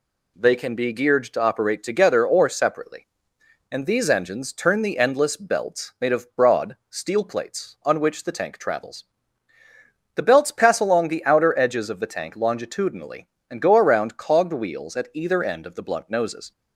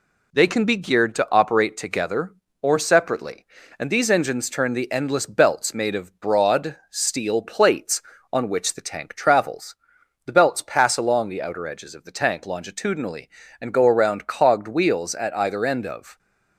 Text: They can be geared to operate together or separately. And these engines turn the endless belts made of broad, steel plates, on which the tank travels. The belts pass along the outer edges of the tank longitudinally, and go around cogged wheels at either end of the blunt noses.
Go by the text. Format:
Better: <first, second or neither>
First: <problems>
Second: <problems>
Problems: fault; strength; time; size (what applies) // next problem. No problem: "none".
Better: first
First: none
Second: stops before "the blunt noses"; at 16.1 s